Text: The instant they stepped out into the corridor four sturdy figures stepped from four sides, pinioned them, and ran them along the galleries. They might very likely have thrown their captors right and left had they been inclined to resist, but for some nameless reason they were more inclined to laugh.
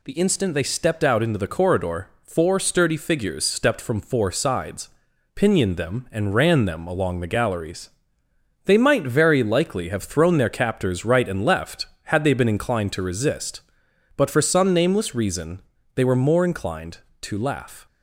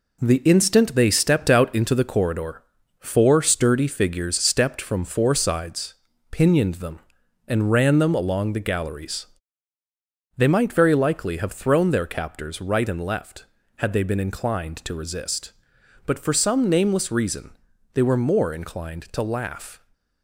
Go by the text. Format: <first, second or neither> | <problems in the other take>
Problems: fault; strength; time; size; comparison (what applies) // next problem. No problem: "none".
first | gets quieter; noticeable; throughout; 6 dB // pauses between "corridor" and "four"; slight; at 2.6 s; 0.34 s long; slight in the first // pauses between "reason" and "they"; slight; at 17.5 s; 0.36 s long; slight in the first